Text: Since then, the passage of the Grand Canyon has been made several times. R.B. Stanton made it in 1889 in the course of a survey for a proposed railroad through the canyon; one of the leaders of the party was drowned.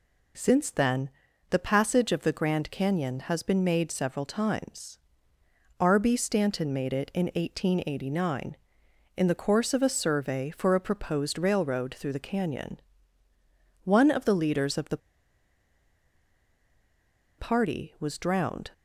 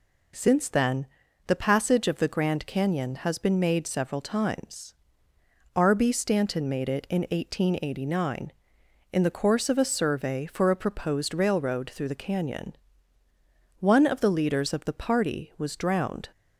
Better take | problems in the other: second | pauses between "the" and "party"; strong; at 14.9 s; 2.3 s long

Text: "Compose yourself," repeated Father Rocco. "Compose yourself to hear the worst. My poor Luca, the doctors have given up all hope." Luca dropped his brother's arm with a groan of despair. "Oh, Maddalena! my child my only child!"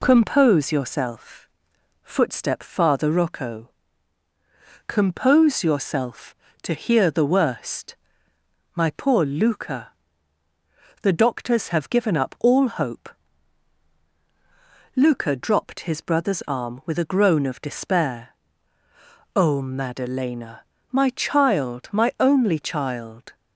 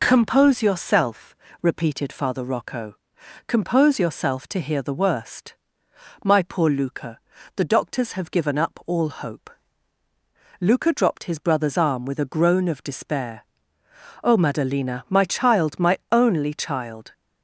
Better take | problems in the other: second | says "footstep" for "repeated"; at 2.0 s

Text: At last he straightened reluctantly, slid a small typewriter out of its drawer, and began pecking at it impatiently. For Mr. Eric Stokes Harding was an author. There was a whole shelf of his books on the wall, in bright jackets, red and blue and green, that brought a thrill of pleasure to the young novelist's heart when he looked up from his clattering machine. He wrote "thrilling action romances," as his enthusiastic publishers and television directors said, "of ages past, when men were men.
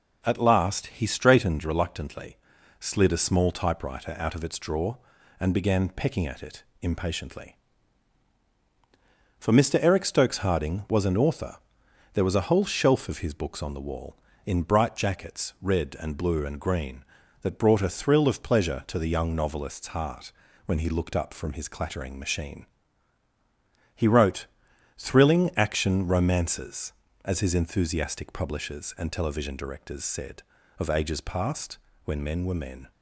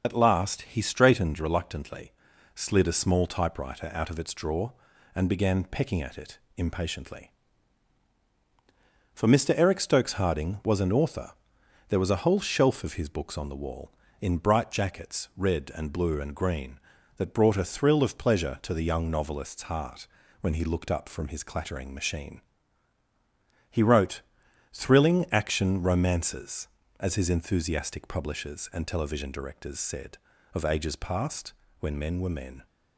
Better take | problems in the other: first | loses the start of "At"; at 0.0 s; 60 ms // pauses between "it" and "impatiently"; slight; at 6.3 s; 0.18 s long; slight in the first // pauses between "heart" and "when"; slight; at 20.0 s; 0.36 s long; slight in the first // pauses between "wrote" and "thrilling"; noticeable; at 24.1 s; 0.54 s long; noticeable in the first

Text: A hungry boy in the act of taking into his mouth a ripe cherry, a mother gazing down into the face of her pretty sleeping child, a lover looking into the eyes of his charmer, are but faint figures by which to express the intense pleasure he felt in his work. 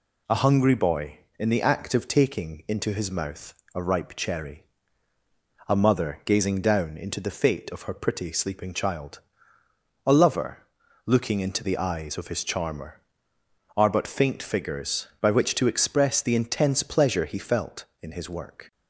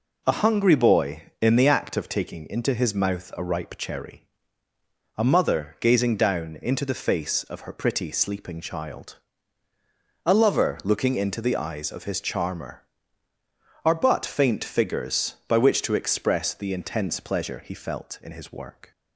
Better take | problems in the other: second | pauses between "mouth" and "a"; slight; at 3.5 s; 0.22 s long // says "fate" for "face"; at 7.2 s // pauses between "lover" and "looking"; at 10.6 s; 0.42 s long

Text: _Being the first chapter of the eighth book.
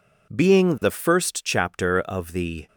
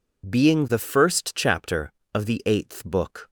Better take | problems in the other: second | stops before "eighth book"; at 2.6 s

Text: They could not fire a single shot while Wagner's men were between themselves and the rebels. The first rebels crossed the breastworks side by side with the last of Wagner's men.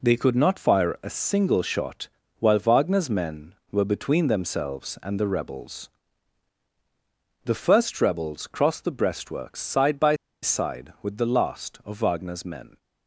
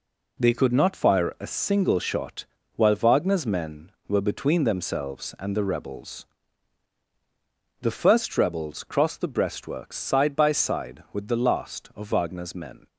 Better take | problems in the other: second | pauses between "shot" and "while"; slight; at 2.0 s; 0.32 s long; slight in the second // pauses between "by" and "side"; slight; at 10.1 s; 0.27 s long

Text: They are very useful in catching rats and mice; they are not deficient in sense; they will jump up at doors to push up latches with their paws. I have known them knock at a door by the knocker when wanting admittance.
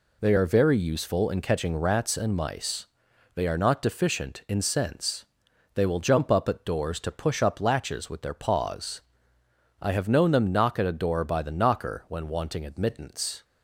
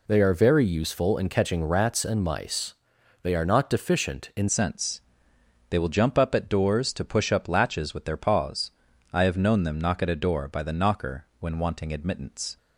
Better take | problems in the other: first | changes voice at "sense"; from 4.4 s on; 8.1 s long

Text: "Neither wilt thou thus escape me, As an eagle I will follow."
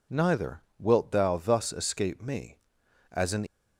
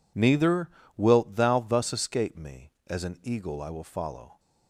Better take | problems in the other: second | pauses between "Neither" and "wilt"; slight; at 0.6 s; 0.18 s long; slight in the second // stops before "eagle I will follow"; at 3.4 s

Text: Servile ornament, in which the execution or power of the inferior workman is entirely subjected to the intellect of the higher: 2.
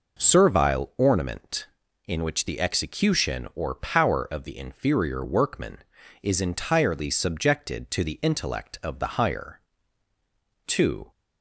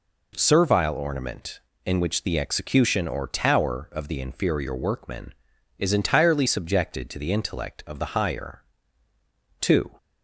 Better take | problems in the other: first | says "tower" for "power"; at 3.2 s

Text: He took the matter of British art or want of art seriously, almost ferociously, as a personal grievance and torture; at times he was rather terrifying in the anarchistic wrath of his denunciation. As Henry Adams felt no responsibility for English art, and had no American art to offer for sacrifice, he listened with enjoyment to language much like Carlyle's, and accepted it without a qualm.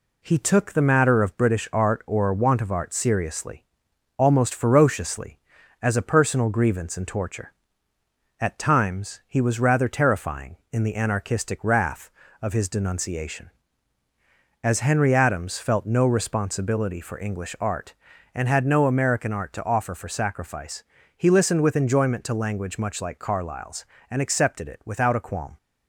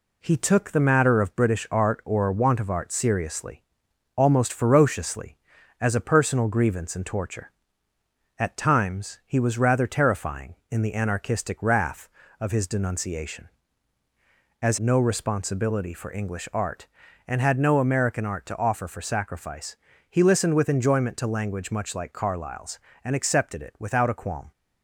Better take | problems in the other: first | skips "Henry Adams felt"; at 14.7 s

